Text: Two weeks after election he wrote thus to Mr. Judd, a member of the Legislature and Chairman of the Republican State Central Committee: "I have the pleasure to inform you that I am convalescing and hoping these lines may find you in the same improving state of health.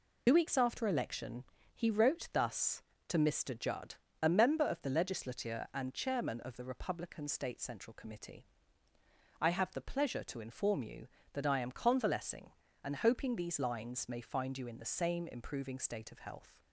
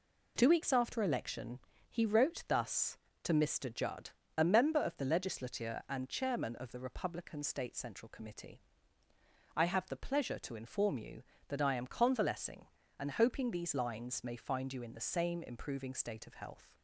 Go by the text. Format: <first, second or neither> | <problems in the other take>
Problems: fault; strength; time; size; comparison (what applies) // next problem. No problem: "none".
second | loses the start of "Two"; at 0.2 s; 65 ms // pauses between "election" and "he"; slight; at 1.4 s; 0.30 s long; slight in the second